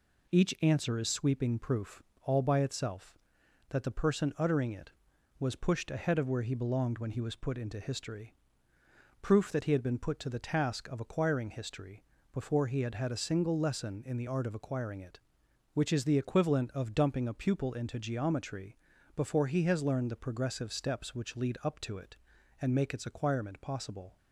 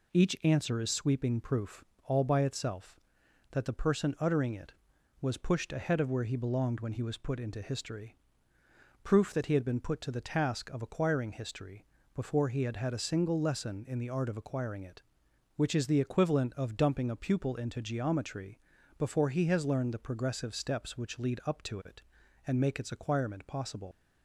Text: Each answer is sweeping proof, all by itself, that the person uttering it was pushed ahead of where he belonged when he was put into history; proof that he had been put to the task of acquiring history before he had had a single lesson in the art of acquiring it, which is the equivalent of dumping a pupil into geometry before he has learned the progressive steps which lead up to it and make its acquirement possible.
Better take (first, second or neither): first